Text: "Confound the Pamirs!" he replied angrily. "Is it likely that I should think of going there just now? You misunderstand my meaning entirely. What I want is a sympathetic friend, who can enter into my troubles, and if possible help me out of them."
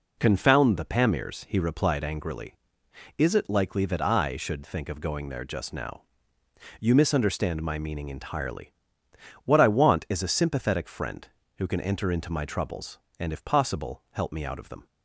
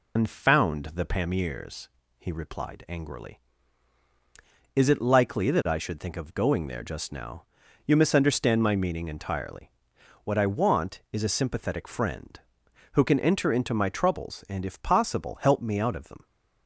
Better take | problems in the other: first | loses the start of "Confound"; at 0.1 s; 115 ms

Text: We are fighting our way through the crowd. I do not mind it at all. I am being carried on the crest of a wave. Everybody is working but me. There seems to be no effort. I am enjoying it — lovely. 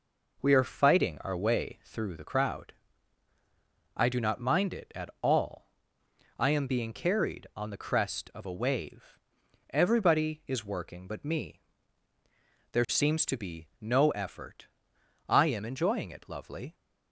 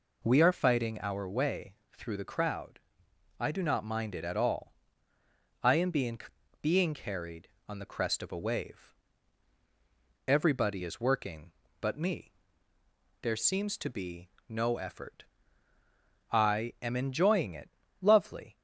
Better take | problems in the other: first | pauses between "way" and "through"; slight; at 1.7 s; 0.22 s long // says "being" twice; at 6.6 s // pauses between "be" and "no"; slight; at 14.2 s; 0.20 s long

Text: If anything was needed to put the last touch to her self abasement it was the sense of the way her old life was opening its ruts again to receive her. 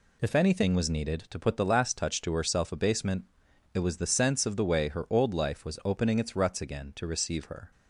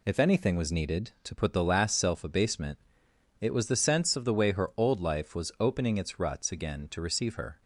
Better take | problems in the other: first | skips "touch to her"; at 1.9 s // pauses between "abasement" and "it"; noticeable; at 2.7 s; 0.62 s long; noticeable in the first

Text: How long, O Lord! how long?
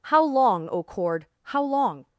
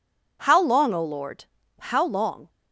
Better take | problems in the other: second | says "Cord" for "Lord"; at 0.8 s

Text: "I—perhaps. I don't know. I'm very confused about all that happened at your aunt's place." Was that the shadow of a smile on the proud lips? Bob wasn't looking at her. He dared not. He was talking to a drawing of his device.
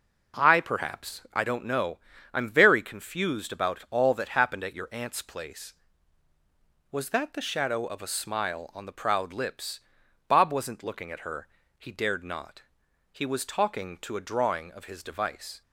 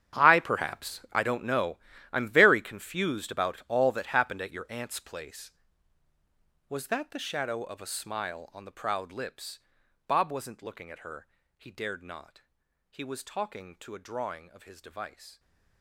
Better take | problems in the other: first | gets quieter; strong; throughout; 16.5 dB

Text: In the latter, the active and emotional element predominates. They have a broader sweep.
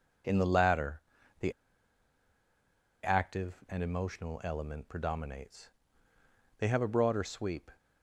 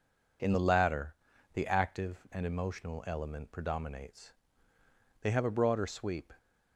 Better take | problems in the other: second | pauses between "the" and "active"; strong; at 1.5 s; 1.5 s long

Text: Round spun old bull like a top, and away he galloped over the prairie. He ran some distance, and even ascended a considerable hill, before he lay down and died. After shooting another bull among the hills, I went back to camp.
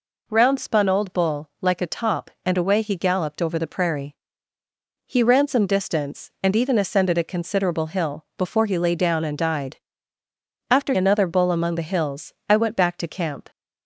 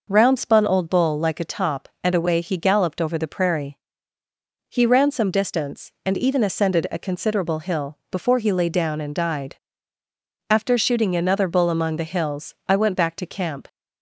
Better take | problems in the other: second | skips "shooting"; at 10.9 s

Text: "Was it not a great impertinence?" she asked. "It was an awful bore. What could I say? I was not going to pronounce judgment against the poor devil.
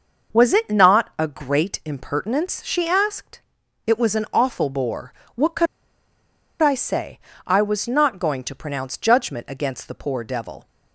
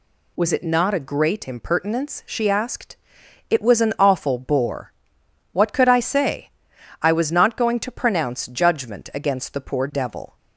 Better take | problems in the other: second | pauses between "could" and "I"; noticeable; at 5.6 s; 0.93 s long

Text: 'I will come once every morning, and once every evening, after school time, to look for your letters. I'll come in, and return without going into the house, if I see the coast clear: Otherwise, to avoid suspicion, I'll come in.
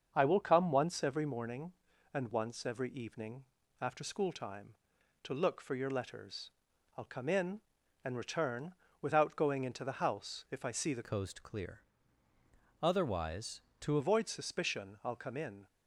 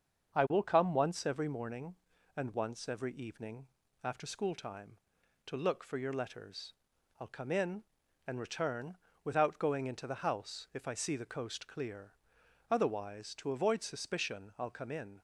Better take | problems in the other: second | starts louder than the rest; until 1.1 s; 7 dB; also in the second // pauses between "return" and "without"; slight; at 8.7 s; 0.26 s long; slight in the second // changes voice from "coast" to "to"; from 11.0 to 13.9 s; 2.9 s long

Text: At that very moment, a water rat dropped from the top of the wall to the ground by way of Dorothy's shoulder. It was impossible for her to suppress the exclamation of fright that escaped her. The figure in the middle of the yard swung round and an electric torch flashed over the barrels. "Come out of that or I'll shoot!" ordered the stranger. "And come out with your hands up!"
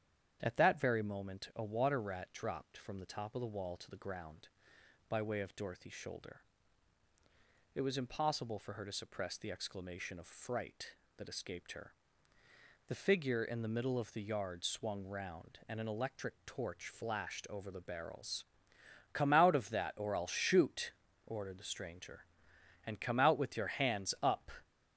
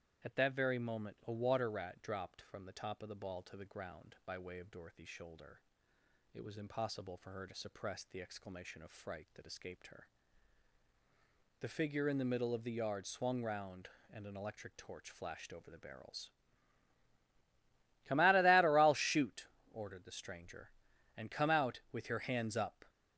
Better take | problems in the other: first | starts louder than the rest; strong; until 1.3 s; 10 dB; strong in the first // says "ball" for "wall"; at 3.1 s

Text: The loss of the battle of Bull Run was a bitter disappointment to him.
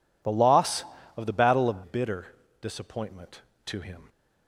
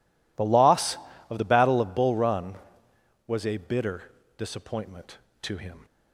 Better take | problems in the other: second | skips "Bull Run was a"; at 1.8 s // pauses between "bitter" and "disappointment"; slight; at 2.2 s; 0.34 s long; slight in the second

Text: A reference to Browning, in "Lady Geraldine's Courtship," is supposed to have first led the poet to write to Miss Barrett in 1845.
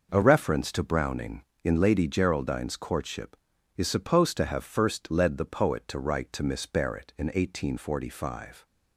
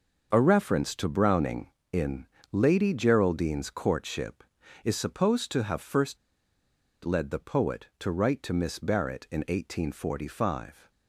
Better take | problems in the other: first | starts louder than the rest; noticeable; until 1.3 s; 6 dB // pauses between "in" and "Lady"; slight; at 2.2 s; 0.26 s long // pauses between "first" and "led"; noticeable; at 6.1 s; 0.86 s long

